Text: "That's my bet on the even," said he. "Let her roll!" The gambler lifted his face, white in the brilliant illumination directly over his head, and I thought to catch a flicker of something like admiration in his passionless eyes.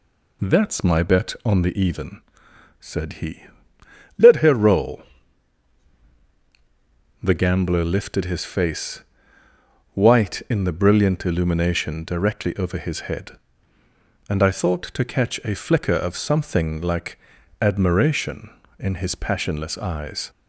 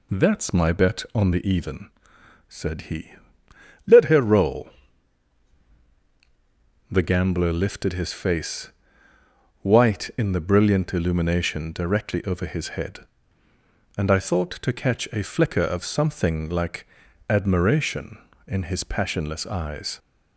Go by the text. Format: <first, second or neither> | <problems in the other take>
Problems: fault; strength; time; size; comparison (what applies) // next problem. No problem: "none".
neither | pauses between "like" and "admiration"; the same in both